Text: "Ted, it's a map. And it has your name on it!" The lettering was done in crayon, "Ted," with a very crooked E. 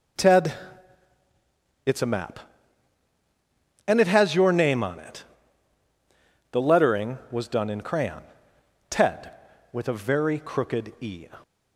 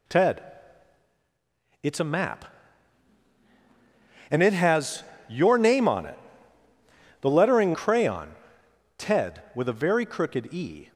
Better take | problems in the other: first | pauses between "has" and "your"; slight; at 5.0 s; 0.24 s long // skips "was done in"; at 7.7 s

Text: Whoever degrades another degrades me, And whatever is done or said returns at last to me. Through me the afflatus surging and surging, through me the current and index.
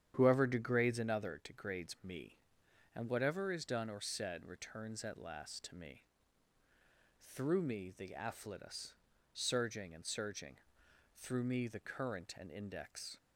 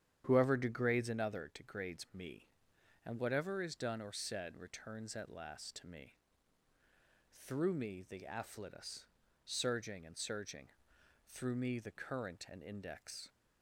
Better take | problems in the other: neither | starts louder than the rest; strong; the same in both // pauses between "afflatus" and "surging"; the same in both

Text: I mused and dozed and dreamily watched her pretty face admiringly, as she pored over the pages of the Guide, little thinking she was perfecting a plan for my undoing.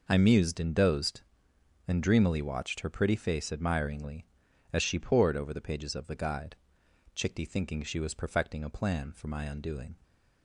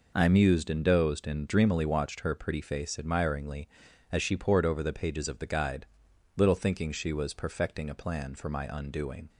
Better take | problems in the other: second | says "chickty" for "little"; at 7.1 s

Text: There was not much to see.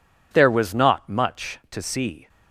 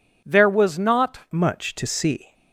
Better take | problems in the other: first | changes voice at "much"; from 1.3 s on; 1.0 s long

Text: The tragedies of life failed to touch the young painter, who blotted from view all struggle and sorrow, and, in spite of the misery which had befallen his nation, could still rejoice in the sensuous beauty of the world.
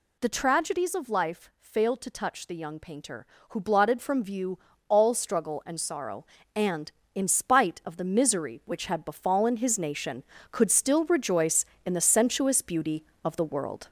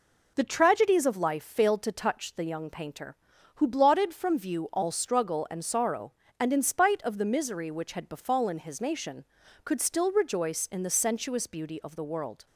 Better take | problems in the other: second | gets louder; noticeable; throughout; 5 dB // pauses between "view" and "all"; slight; at 4.5 s; 0.30 s long

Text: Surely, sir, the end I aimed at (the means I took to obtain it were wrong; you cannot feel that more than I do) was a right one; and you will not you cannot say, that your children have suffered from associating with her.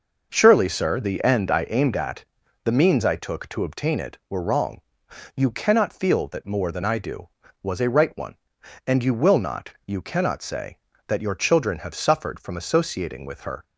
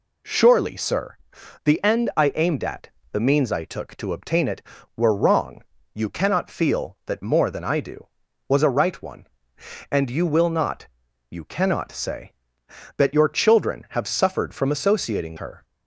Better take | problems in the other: first | pauses between "not" and "you"; at 10.8 s; 0.42 s long; slight in the first // skips "with"; at 15.3 s

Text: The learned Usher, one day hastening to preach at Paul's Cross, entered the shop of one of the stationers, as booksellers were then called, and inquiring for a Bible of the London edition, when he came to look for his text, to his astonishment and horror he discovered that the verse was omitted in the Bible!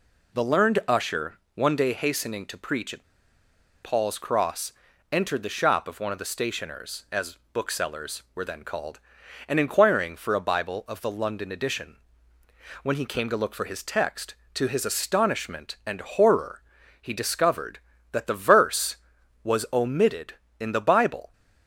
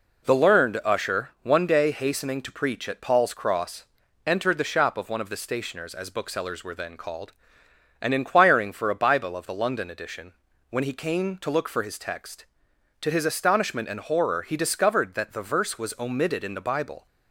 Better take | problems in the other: second | pauses between "at" and "Paul's"; noticeable; at 3.0 s; 0.78 s long // pauses between "as" and "booksellers"; slight; at 7.3 s; 0.16 s long // pauses between "horror" and "he"; at 16.6 s; 0.40 s long

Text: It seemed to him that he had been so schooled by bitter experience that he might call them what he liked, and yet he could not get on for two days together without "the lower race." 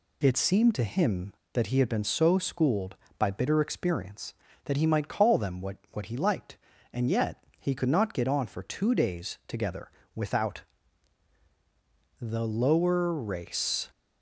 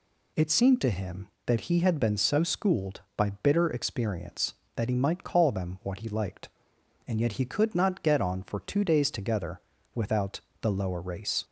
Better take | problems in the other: second | says "what" twice; at 5.9 s // pauses between "yet" and "he"; slight; at 7.4 s; 0.16 s long // pauses between "together" and "without"; slight; at 9.8 s; 0.24 s long; slight in the second // pauses between "without" and "the"; strong; at 10.6 s; 1.5 s long; slight in the second

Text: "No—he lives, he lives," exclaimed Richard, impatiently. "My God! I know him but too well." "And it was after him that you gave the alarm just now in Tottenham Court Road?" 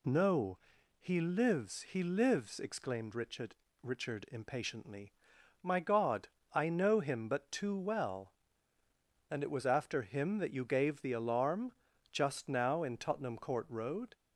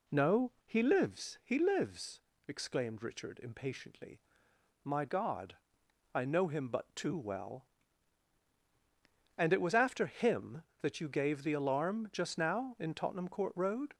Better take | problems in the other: second | says "Richard" twice; at 3.8 s // pauses between "alarm" and "just"; at 11.7 s; 0.40 s long

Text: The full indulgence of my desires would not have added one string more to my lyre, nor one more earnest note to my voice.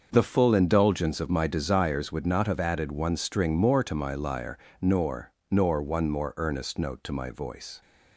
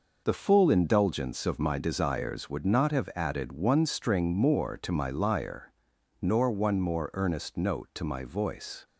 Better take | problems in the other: second | starts louder than the rest; until 1.1 s; 6.5 dB // says "nor" twice; at 5.5 s

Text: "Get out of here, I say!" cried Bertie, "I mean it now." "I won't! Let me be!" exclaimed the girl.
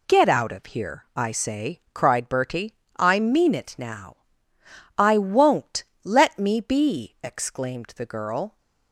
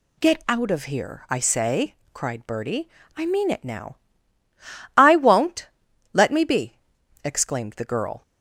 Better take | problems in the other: neither | none

